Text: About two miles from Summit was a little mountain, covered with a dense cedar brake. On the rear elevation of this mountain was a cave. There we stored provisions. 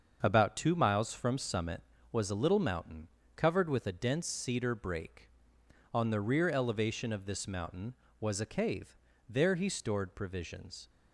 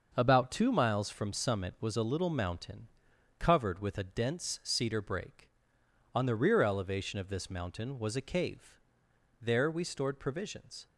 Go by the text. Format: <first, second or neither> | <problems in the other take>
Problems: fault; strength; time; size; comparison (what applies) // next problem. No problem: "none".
second | starts louder than the rest; until 1.2 s; 6.5 dB; also in the second // says "he" for "we"; at 9.5 s